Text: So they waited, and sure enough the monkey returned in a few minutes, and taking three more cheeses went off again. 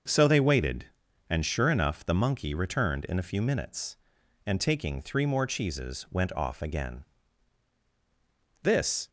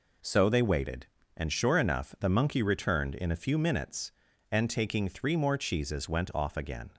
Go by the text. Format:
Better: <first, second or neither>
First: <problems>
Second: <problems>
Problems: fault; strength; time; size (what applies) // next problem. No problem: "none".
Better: second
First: starts louder than the rest; until 1.5 s; 6 dB // goes on to say "This"; slight; from 8.6 s on; 0.46 s long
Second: none